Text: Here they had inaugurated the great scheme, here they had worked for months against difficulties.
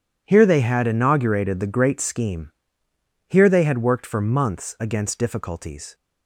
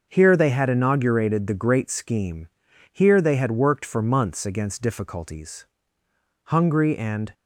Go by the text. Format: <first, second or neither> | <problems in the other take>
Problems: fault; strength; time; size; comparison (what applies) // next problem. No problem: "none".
first | starts louder than the rest; until 1.1 s; 6.5 dB // goes on to say "Hungry and"; noticeable; from 6.4 s on; 0.88 s long